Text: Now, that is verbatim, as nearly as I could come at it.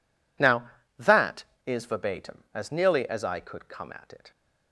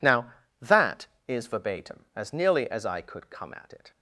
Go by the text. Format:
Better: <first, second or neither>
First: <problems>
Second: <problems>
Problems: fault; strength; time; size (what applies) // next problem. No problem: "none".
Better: neither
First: none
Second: none